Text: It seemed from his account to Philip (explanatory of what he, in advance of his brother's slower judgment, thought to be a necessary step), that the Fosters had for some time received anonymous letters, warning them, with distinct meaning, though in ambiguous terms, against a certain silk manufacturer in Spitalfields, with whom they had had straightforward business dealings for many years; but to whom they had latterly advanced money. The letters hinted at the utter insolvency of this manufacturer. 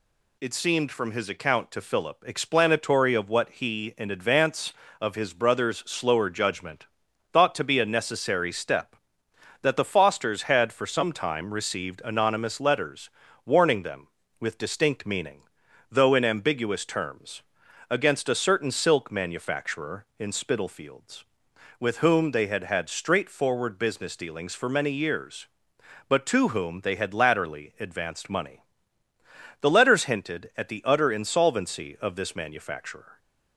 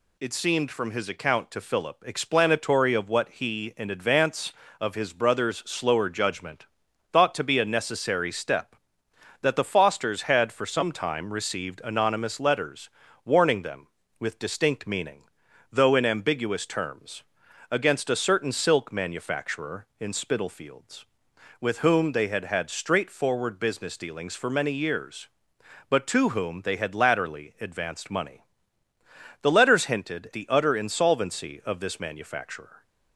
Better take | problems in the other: first | skips "at"; at 30.3 s

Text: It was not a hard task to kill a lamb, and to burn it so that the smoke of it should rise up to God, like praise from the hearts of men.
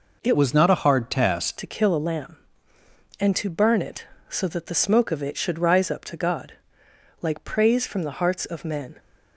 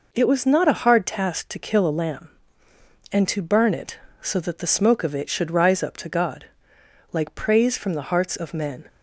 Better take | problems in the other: second | changes voice from "was" to "task"; from 0.3 to 1.5 s; 1.2 s long

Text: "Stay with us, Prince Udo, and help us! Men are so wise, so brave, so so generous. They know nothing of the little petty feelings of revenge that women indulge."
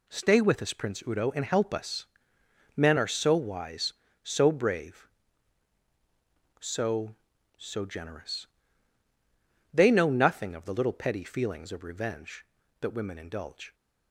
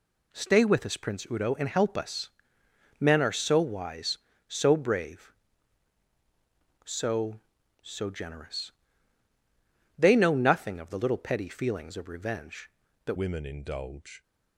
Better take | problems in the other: first | changes voice at "women"; from 13.1 s on; 1.1 s long

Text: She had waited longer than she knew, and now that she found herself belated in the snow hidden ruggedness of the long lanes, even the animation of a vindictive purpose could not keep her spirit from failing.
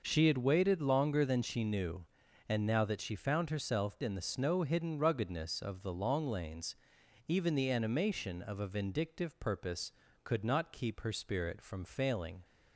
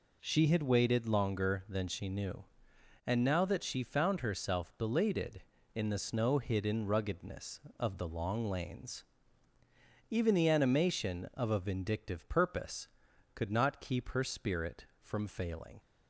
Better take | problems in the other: second | skips "belated"; at 3.9 s

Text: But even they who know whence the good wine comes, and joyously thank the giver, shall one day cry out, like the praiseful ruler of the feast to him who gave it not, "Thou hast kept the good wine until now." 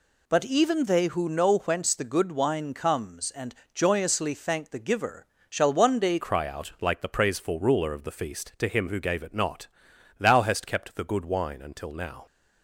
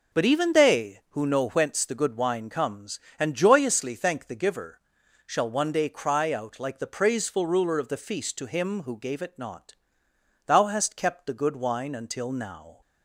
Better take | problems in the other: second | pauses between "and" and "joyously"; slight; at 3.5 s; 0.20 s long // changes voice at "cry"; from 6.1 s on; 6.1 s long

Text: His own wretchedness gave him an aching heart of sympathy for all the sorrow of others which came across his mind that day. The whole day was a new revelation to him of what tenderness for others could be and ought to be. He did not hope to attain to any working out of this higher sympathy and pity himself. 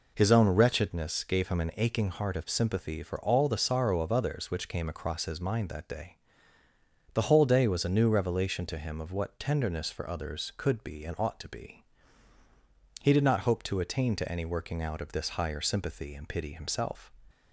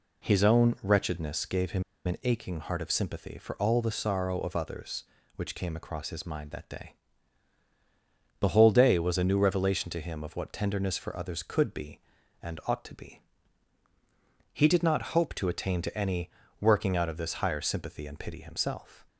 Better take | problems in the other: first | pauses between "him" and "an"; slight; at 1.8 s; 0.22 s long // pauses between "any" and "working"; slight; at 16.2 s; 0.32 s long

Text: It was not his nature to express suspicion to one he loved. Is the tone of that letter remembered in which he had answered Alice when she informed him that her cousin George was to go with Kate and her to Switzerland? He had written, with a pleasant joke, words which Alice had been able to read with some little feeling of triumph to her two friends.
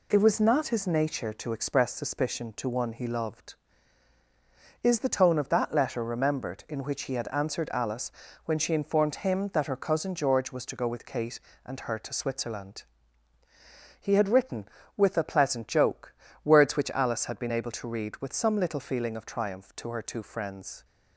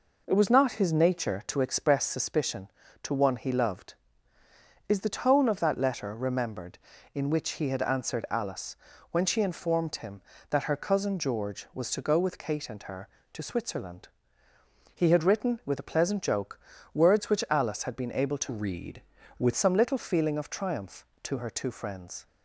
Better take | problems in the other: first | pauses between "Alice" and "when"; slight; at 8.7 s; 0.36 s long; slight in the first // changes voice from "read" to "with"; from 18.4 to 19.5 s; 1.1 s long

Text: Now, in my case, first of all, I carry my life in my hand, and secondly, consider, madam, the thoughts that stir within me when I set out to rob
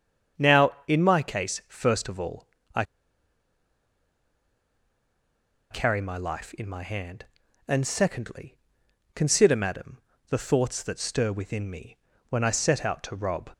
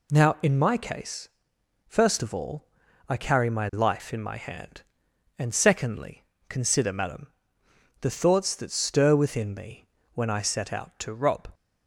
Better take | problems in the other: second | starts louder than the rest; strong; until 1.5 s; 7.5 dB // pauses between "I" and "carry"; strong; at 2.8 s; 2.8 s long // pauses between "me" and "when"; slight; at 11.9 s; 0.32 s long; slight in the second

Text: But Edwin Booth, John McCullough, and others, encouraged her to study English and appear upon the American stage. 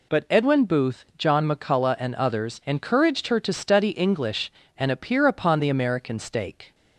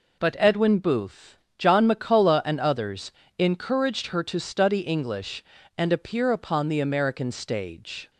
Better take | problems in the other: second | says "stake" for "stage"; at 6.1 s

